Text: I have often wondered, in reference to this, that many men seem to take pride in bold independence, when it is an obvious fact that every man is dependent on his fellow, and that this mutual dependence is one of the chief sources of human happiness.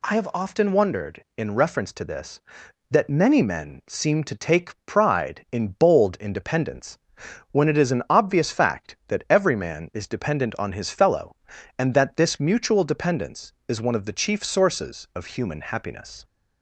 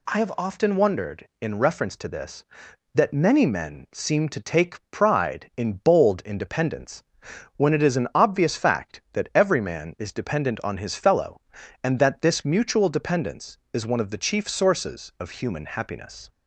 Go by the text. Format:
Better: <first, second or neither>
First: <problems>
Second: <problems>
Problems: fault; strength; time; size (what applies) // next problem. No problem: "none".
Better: neither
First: none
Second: none